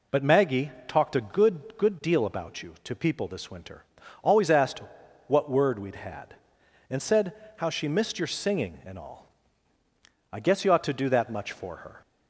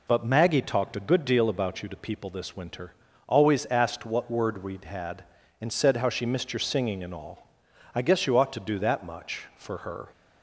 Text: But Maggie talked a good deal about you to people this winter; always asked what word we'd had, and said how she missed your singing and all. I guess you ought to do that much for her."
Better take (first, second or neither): second